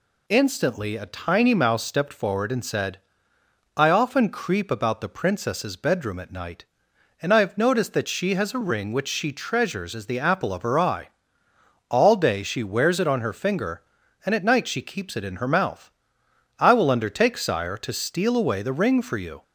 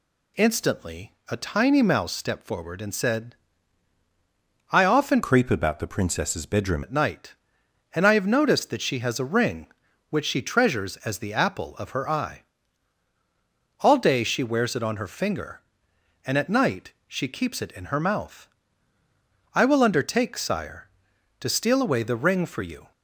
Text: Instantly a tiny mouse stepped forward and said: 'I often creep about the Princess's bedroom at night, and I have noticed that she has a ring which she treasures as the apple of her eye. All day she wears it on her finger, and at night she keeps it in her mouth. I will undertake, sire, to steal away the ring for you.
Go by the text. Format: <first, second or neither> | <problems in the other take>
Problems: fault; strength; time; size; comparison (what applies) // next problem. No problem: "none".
first | pauses between "Instantly" and "a"; slight; at 1.1 s; 0.16 s long // changes voice from "creep" to "bedroom"; from 5.2 to 6.8 s; 1.6 s long // pauses between "night" and "she"; slight; at 16.9 s; 0.16 s long